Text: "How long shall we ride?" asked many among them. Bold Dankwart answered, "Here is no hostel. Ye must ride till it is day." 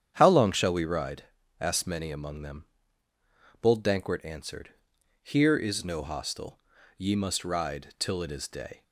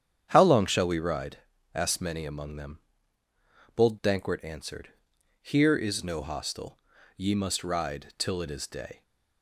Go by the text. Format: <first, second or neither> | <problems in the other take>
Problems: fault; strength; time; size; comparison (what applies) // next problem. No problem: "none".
neither | starts louder than the rest; strong; the same in both